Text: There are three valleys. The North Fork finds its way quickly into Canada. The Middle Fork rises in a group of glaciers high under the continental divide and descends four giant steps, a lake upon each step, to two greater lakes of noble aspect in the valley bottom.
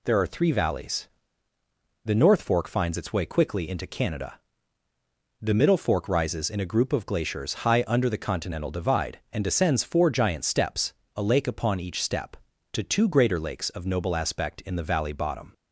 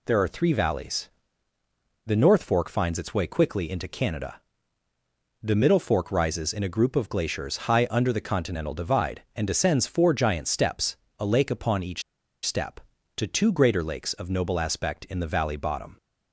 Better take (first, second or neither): first